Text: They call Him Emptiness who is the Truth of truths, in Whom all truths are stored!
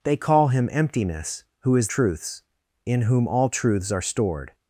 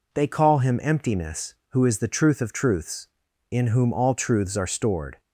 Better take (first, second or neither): second